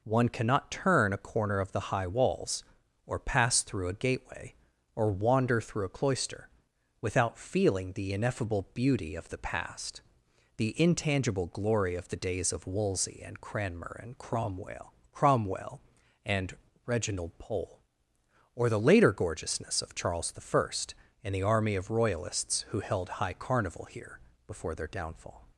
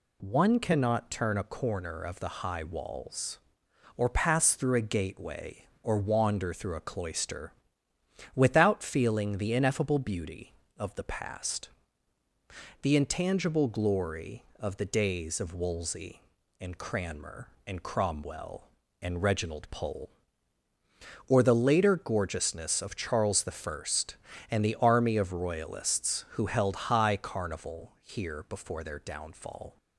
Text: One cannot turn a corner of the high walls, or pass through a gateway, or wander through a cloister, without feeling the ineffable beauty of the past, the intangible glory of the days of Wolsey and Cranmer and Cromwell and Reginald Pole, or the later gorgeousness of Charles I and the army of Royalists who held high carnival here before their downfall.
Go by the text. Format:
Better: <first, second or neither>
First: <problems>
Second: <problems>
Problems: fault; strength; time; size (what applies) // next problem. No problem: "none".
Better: second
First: says "Cromwell" twice; at 15.1 s // pauses between "and" and "Reginald"; slight; at 16.5 s; 0.30 s long // pauses between "here" and "before"; slight; at 24.1 s; 0.28 s long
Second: none